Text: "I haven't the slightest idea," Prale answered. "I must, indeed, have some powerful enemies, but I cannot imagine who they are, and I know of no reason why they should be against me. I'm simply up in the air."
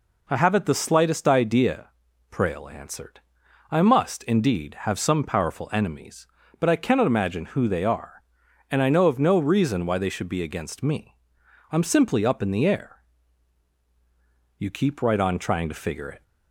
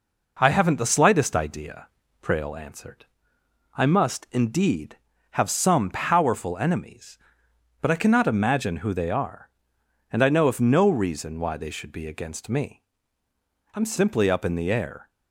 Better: second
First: goes on to say "You keep right on trying to figure it"; from 14.5 s on; 1.6 s long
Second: none

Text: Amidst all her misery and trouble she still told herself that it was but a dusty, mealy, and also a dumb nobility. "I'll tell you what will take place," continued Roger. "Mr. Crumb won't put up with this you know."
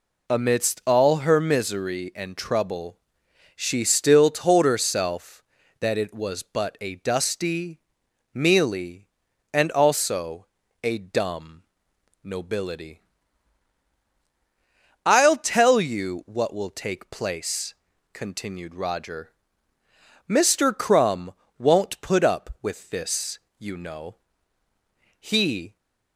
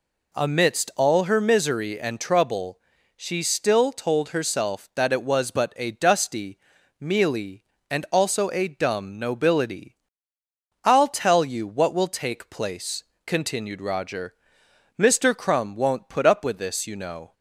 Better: second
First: pauses between "trouble" and "she"; noticeable; at 2.9 s; 0.60 s long // pauses between "also" and "a"; at 10.4 s; 0.38 s long // pauses between "dumb" and "nobility"; noticeable; at 11.6 s; 0.62 s long // pauses between "Crumb" and "won't"; slight; at 21.3 s; 0.24 s long // pauses between "this" and "you"; slight; at 23.3 s; 0.20 s long // goes on to say "He"; from 25.2 s on; 0.56 s long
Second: pauses between "trouble" and "she"; at 2.7 s; 0.40 s long

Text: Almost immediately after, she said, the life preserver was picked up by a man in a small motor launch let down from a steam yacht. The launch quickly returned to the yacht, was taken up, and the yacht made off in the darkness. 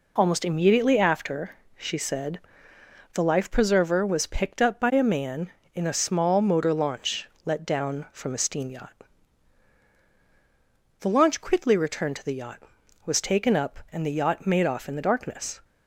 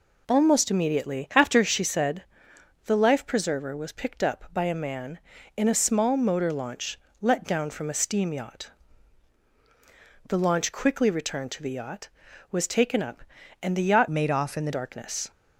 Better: first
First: pauses between "launch" and "let"; slight; at 7.2 s; 0.16 s long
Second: pauses between "launch" and "let"; slight; at 6.9 s; 0.22 s long // changes voice from "made" to "the"; from 14.0 to 14.7 s; 0.7 s long

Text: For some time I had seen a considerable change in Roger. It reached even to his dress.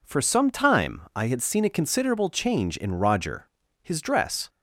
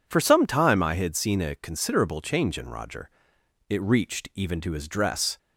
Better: second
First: skips "It reached even to"; at 3.6 s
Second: none

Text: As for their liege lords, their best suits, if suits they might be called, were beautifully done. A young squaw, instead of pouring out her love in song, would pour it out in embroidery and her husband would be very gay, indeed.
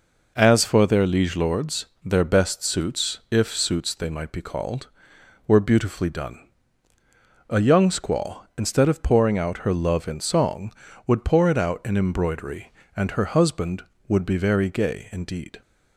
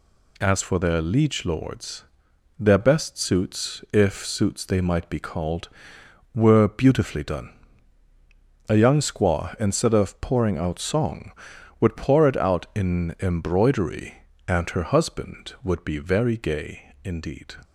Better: first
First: none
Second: skips "her love in"; at 10.7 s

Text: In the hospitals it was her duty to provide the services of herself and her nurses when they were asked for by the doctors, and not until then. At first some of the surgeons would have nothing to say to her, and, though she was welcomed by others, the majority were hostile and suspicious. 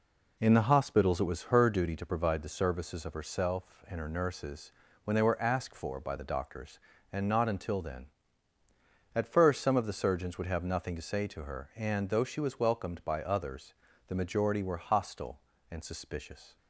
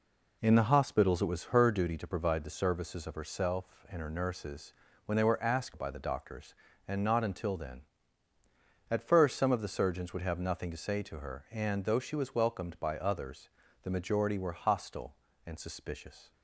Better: first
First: pauses between "nurses" and "when"; slight; at 4.7 s; 0.32 s long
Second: pauses between "nurses" and "when"; slight; at 4.7 s; 0.32 s long // skips "for"; at 5.7 s

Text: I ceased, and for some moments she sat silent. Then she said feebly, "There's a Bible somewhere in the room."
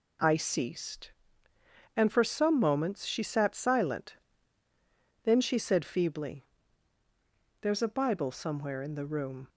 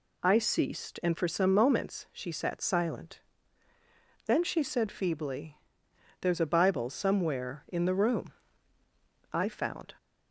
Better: first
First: none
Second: goes on to say "I found"; noticeable; from 9.3 s on; 0.62 s long

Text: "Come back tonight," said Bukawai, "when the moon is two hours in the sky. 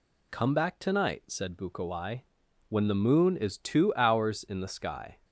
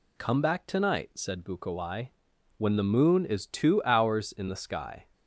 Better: neither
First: none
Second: none

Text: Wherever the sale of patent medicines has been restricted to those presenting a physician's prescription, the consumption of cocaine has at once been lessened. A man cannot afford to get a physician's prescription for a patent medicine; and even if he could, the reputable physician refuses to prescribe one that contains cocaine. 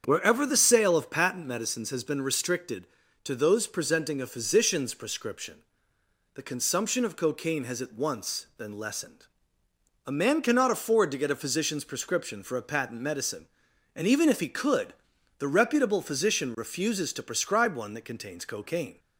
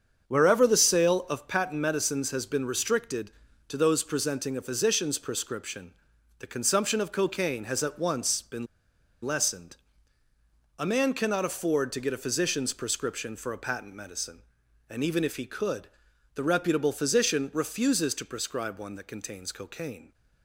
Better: first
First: starts louder than the rest; strong; until 1.0 s; 7.5 dB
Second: starts louder than the rest; strong; until 1.3 s; 7.5 dB // pauses between "been" and "lessened"; noticeable; at 8.6 s; 0.58 s long

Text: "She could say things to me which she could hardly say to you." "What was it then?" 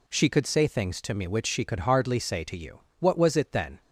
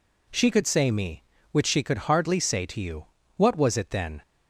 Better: first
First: none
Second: skips "things to"; at 0.9 s

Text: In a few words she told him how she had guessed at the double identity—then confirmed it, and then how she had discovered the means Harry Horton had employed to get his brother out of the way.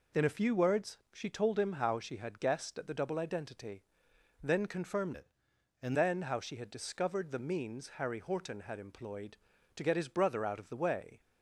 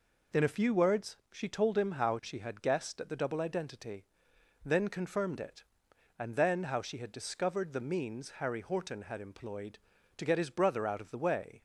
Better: second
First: changes voice from "it" to "and"; from 5.1 to 5.9 s; 0.8 s long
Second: none

